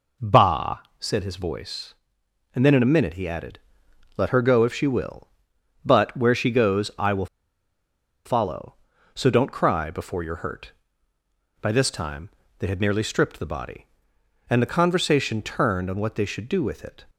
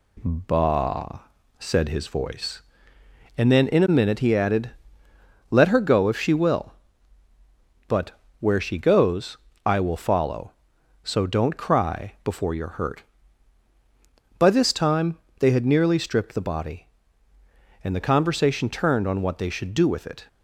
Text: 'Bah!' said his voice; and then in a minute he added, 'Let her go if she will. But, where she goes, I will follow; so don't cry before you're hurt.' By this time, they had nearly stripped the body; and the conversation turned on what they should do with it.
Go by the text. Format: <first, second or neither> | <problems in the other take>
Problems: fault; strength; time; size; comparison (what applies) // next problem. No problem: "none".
second | pauses between "will" and "follow"; at 7.2 s; 0.99 s long